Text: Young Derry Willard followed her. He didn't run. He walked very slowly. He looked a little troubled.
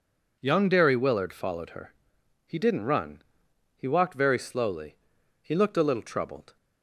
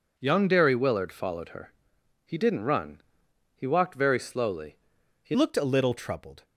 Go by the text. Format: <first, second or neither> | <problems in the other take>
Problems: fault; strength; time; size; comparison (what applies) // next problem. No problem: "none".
first | changes voice at "looked"; from 5.3 s on; 1.1 s long